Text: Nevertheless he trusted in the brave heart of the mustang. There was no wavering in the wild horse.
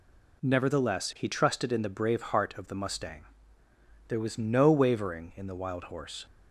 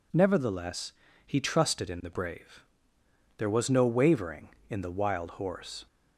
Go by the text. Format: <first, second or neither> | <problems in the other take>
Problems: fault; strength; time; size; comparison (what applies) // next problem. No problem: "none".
first | pauses between "Nevertheless" and "he"; slight; at 0.9 s; 0.32 s long // skips "heart of the mustang"; at 3.0 s